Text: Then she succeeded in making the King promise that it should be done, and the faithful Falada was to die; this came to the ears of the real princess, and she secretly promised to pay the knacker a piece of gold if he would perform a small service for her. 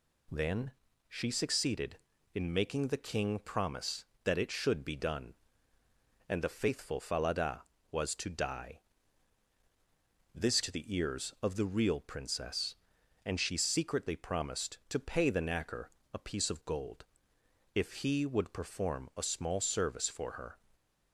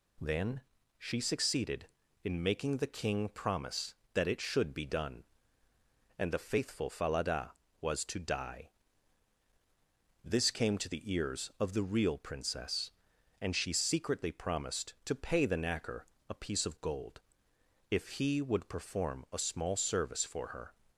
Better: second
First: pauses between "Then" and "she"; slight; at 0.7 s; 0.36 s long // skips "came"; at 10.6 s // pauses between "knacker" and "a"; slight; at 15.8 s; 0.22 s long // pauses between "gold" and "if"; noticeable; at 17.0 s; 0.72 s long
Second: pauses between "Then" and "she"; slight; at 0.6 s; 0.36 s long // pauses between "knacker" and "a"; slight; at 16.0 s; 0.22 s long // pauses between "gold" and "if"; noticeable; at 17.1 s; 0.72 s long

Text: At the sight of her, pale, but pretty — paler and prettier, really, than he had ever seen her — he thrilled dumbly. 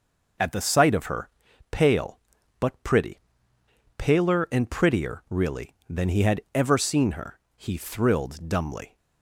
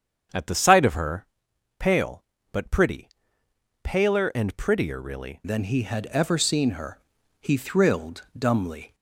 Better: first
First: none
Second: starts louder than the rest; strong; until 1.8 s; 7.5 dB // changes voice at "than"; from 5.4 s on; 3.5 s long

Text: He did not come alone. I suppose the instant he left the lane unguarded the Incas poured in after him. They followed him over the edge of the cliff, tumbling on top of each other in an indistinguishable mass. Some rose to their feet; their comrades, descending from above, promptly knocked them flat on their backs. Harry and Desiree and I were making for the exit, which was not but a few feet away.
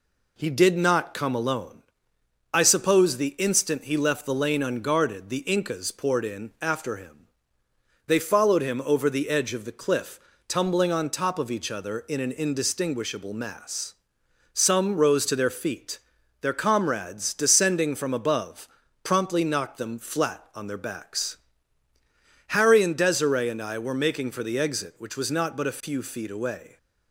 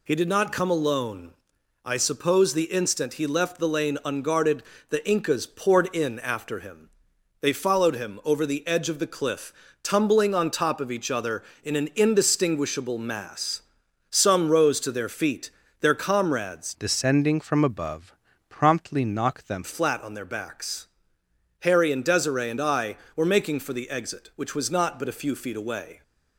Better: first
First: none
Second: pauses between "unguarded" and "the"; slight; at 4.6 s; 0.26 s long // changes voice from "descending" to "them"; from 16.8 to 19.6 s; 2.8 s long

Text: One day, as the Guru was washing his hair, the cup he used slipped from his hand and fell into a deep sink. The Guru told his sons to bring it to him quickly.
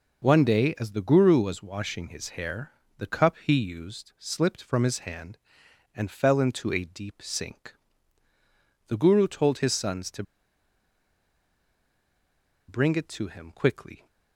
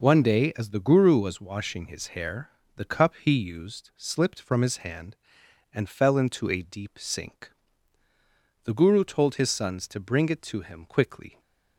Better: second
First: pauses between "to" and "bring"; strong; at 10.2 s; 2.4 s long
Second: none

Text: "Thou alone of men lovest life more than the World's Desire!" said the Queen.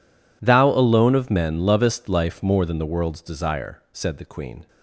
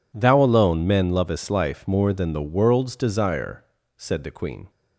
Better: first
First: none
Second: skips "of"; at 0.8 s

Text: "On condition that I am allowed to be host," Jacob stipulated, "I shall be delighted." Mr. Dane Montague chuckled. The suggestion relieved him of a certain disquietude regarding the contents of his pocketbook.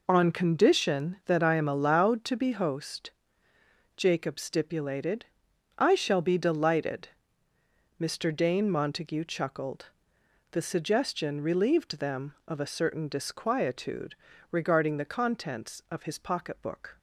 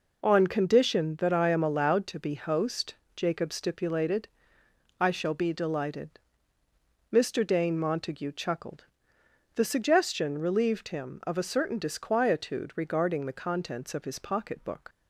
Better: second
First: says "them" for "him"; at 11.9 s // pauses between "disquietude" and "regarding"; at 14.1 s; 0.38 s long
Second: none

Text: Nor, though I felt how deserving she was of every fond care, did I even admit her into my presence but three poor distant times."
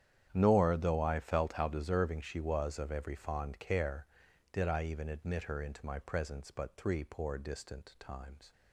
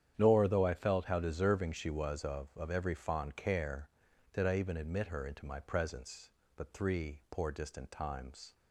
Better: first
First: starts louder than the rest; strong; until 1.3 s; 9.5 dB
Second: starts louder than the rest; strong; until 1.1 s; 9.5 dB // says "of" twice; at 2.5 s

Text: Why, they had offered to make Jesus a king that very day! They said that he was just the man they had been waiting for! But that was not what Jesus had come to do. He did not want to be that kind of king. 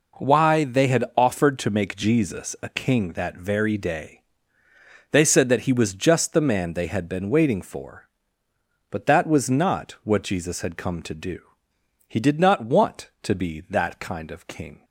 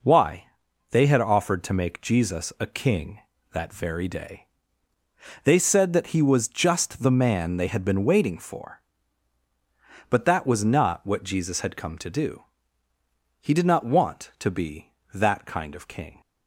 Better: neither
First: none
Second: none

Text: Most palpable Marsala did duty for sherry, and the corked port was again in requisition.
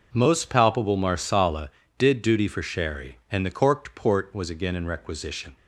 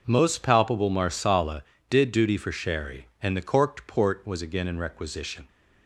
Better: neither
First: none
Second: none

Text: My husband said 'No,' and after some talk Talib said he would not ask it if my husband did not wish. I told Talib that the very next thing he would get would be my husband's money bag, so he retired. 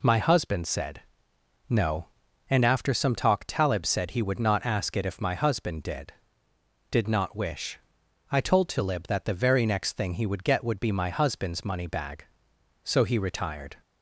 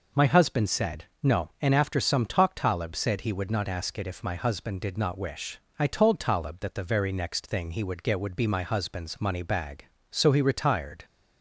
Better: second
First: pauses between "said" and "No"; noticeable; at 1.0 s; 0.68 s long // says "did" twice; at 6.8 s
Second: pauses between "said" and "No"; slight; at 1.0 s; 0.18 s long

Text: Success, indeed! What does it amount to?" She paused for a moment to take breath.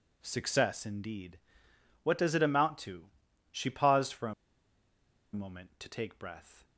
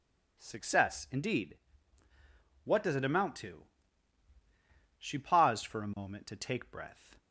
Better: second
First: pauses between "a" and "moment"; at 4.3 s; 1.0 s long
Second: none

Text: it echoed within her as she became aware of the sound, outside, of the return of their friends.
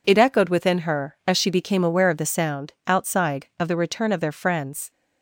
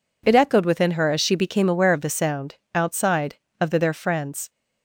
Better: first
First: none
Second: skips "return of"; at 3.7 s

